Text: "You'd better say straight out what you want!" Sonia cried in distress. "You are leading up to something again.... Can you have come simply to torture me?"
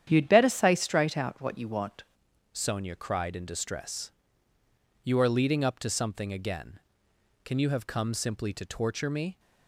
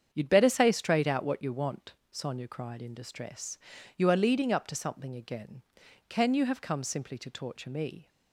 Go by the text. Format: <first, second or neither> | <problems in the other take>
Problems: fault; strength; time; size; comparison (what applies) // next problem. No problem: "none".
second | starts louder than the rest; strong; until 1.0 s; 9.5 dB; strong in the second // changes voice at "Sonia"; from 2.5 s on; 6.8 s long